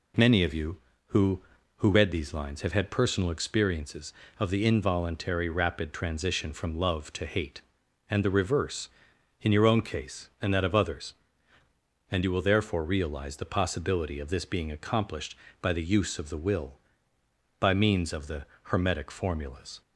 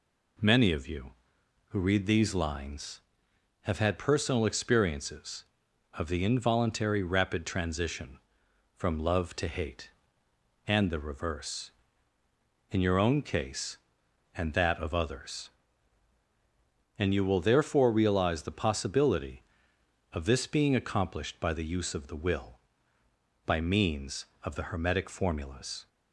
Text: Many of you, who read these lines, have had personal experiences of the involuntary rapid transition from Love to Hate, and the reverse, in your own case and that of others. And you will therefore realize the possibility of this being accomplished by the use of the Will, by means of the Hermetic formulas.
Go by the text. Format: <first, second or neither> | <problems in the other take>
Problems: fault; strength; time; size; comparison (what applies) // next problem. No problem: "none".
second | says "who" twice; at 1.7 s // pauses between "the" and "Hermetic"; slight; at 18.4 s; 0.24 s long